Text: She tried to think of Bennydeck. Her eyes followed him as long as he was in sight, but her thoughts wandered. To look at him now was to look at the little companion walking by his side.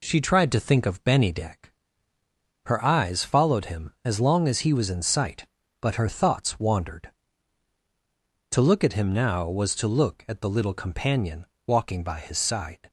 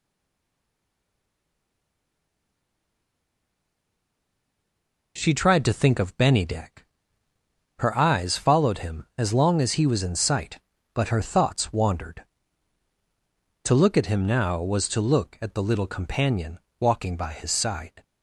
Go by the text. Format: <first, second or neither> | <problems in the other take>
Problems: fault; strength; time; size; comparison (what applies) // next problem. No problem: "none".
first | stays silent before the first word; strong; until 5.1 s; 5.1 s long // pauses between "companion" and "walking"; slight; at 16.5 s; 0.22 s long; slight in the first